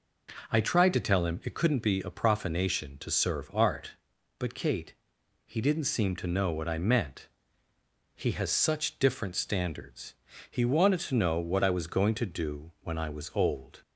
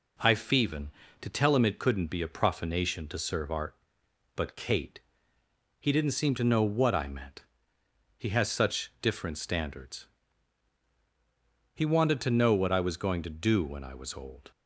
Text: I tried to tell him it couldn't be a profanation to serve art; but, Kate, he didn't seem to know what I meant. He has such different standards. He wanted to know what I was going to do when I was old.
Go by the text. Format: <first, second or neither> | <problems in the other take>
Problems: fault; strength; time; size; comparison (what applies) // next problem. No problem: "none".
first | says "feven" for "tried"; at 0.3 s